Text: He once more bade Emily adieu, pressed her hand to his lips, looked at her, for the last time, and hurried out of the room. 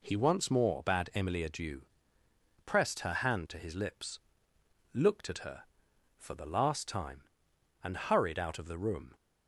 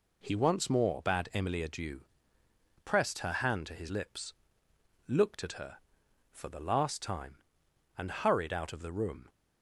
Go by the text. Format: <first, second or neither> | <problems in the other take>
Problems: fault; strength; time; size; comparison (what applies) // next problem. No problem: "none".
neither | none